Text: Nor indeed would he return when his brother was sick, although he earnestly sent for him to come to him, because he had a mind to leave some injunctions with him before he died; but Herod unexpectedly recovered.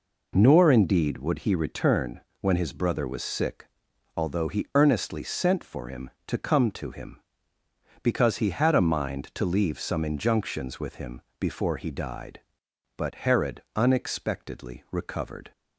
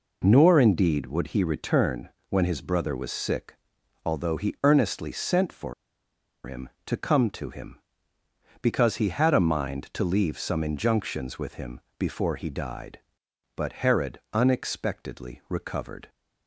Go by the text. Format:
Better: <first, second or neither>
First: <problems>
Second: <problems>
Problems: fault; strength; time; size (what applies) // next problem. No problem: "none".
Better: first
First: pauses between "return" and "when"; slight; at 2.2 s; 0.20 s long // pauses between "him" and "before"; slight; at 11.2 s; 0.18 s long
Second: pauses between "return" and "when"; slight; at 2.0 s; 0.20 s long // pauses between "for" and "him"; noticeable; at 5.7 s; 0.71 s long // pauses between "him" and "before"; slight; at 11.7 s; 0.18 s long